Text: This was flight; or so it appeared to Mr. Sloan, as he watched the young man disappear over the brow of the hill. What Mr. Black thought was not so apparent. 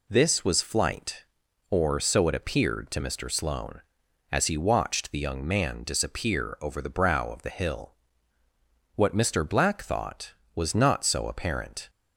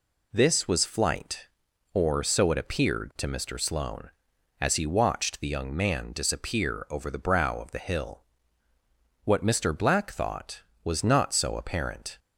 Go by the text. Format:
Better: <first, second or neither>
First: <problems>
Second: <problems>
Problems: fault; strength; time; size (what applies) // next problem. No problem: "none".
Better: neither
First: none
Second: none